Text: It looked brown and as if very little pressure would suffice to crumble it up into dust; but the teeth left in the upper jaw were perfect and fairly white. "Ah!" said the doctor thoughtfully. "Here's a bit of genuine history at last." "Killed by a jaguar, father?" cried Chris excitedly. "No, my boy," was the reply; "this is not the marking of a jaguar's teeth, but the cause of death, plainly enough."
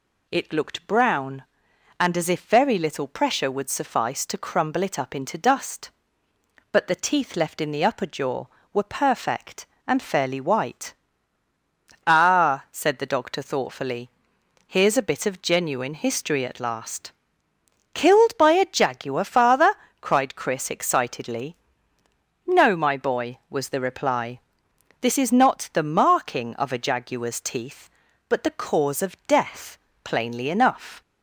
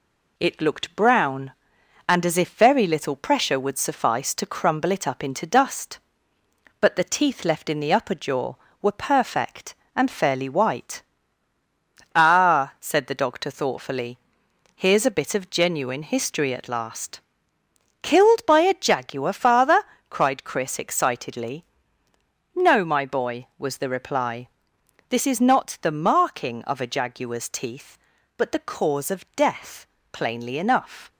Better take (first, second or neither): first